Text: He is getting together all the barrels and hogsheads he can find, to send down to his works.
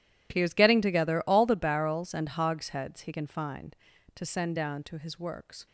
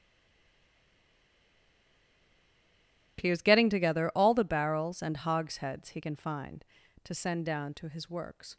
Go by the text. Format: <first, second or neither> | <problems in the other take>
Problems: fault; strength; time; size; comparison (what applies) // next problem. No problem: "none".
first | stays silent before the first word; strong; until 3.1 s; 3.1 s long